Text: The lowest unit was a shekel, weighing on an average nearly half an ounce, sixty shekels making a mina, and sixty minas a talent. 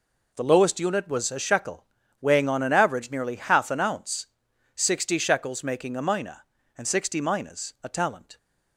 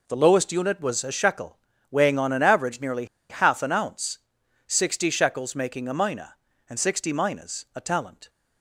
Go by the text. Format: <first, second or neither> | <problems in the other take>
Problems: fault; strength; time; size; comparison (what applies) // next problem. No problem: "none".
first | pauses between "nearly" and "half"; slight; at 3.0 s; 0.24 s long